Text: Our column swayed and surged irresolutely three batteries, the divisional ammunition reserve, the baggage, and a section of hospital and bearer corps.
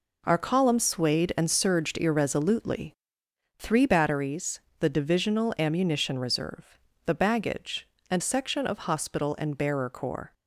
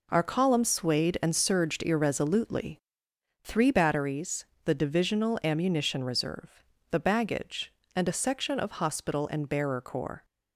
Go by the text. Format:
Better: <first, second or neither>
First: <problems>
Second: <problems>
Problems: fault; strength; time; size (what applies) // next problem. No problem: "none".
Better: second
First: pauses between "irresolutely" and "three"; noticeable; at 2.9 s; 0.64 s long // skips "a"; at 8.2 s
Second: pauses between "irresolutely" and "three"; noticeable; at 2.7 s; 0.64 s long